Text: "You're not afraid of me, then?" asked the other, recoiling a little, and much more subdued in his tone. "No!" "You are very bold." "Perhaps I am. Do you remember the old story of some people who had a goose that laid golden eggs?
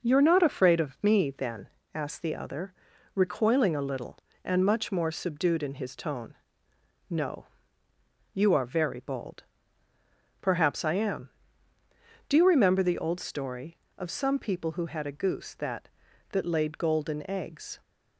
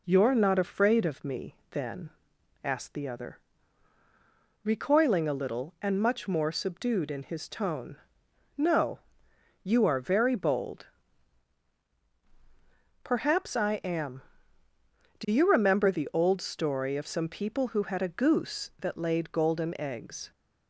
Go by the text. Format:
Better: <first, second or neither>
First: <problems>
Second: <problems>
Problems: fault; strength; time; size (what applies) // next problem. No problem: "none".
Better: second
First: says "that" twice; at 16.2 s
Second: none